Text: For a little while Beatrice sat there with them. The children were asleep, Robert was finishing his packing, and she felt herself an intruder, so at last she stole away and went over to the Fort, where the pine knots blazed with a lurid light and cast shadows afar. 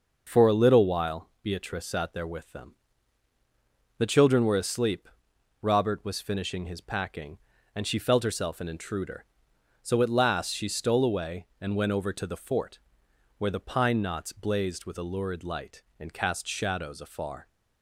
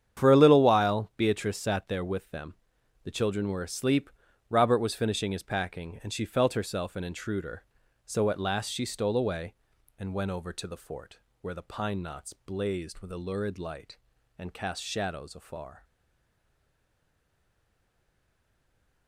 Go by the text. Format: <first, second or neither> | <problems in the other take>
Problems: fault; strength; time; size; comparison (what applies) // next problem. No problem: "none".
first | starts louder than the rest; strong; until 1.2 s; 8.5 dB // stays silent after the last word; strong; from 15.8 s on; 3.2 s long